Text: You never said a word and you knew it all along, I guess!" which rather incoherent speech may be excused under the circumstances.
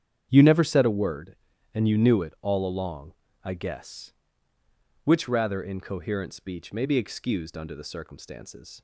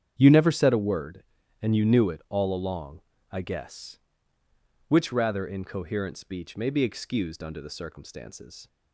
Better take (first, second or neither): neither